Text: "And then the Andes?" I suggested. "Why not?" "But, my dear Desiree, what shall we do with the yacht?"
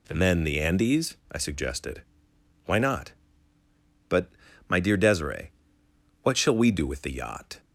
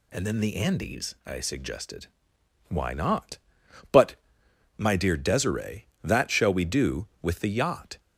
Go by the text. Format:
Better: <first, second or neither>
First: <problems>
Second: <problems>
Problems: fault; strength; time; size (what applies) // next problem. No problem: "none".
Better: first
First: none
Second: says "that" for "what"; at 6.0 s